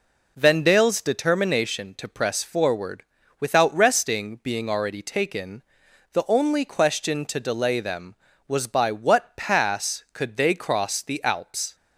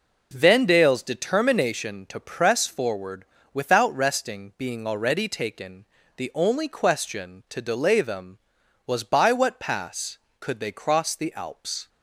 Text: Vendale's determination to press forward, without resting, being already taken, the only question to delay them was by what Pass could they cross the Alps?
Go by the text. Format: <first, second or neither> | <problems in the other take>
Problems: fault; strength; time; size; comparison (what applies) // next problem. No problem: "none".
neither | none